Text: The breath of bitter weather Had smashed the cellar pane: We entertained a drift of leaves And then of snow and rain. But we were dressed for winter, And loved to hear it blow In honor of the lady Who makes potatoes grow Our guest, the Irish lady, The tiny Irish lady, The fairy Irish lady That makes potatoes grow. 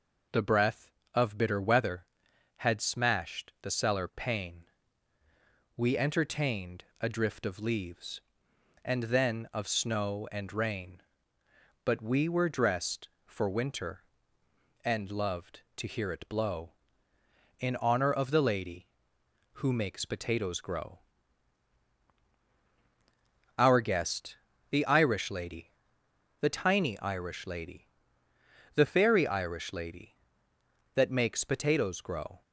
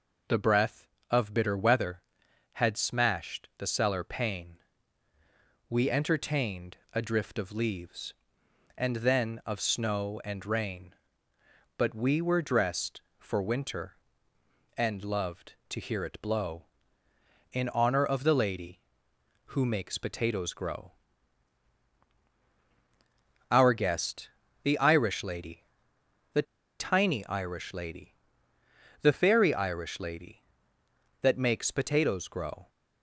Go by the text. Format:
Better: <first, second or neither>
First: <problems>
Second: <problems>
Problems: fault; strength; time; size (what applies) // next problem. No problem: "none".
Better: first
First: pauses between "entertained" and "a"; slight; at 6.8 s; 0.18 s long // pauses between "grow" and "Our"; strong; at 20.9 s; 2.5 s long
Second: pauses between "entertained" and "a"; slight; at 6.7 s; 0.18 s long // pauses between "grow" and "Our"; strong; at 20.9 s; 2.5 s long // pauses between "The" and "tiny"; at 26.4 s; 0.36 s long